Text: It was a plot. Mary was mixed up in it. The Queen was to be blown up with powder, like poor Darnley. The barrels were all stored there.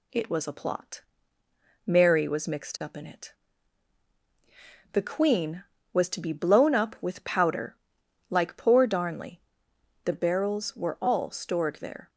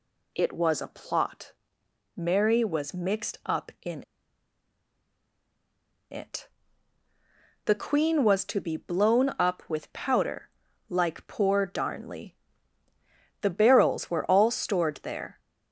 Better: first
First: none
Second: pauses between "in" and "it"; strong; at 4.0 s; 2.0 s long

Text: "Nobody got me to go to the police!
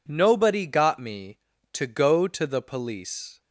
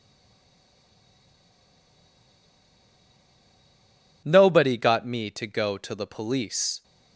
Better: first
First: none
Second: stays silent before the first word; strong; until 4.2 s; 4.2 s long

